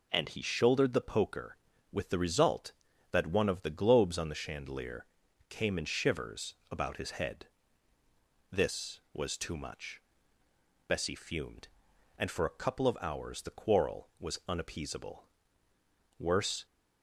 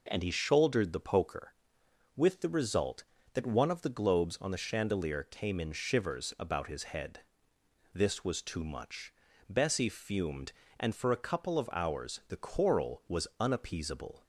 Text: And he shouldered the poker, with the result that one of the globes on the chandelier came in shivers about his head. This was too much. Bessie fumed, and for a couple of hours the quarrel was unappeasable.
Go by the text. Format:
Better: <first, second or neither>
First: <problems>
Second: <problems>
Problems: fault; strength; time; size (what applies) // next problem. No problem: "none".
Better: second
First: pauses between "chandelier" and "came"; at 5.0 s; 0.44 s long // pauses between "shivers" and "about"; slight; at 6.5 s; 0.16 s long // goes on to say "Worse"; slight; from 16.1 s on; 0.48 s long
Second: none